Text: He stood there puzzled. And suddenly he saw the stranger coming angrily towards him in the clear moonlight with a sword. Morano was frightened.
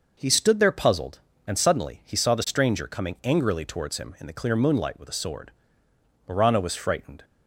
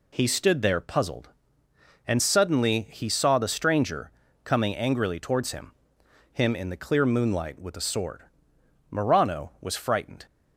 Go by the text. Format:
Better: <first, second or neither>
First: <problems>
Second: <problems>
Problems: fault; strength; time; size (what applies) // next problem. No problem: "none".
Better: first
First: none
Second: pauses between "stranger" and "coming"; slight; at 4.1 s; 0.34 s long // says "him" twice; at 6.3 s